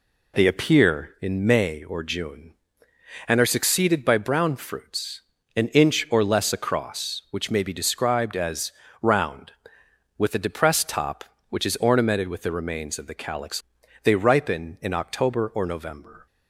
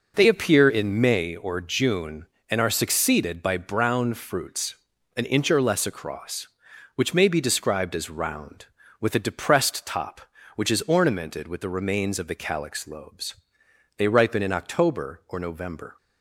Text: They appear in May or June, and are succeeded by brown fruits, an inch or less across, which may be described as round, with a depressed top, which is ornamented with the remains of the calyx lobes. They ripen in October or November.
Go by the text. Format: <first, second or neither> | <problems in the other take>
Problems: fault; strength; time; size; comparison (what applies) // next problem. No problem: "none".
second | pauses between "as" and "round"; slight; at 8.7 s; 0.28 s long // skips "lobes"; at 13.8 s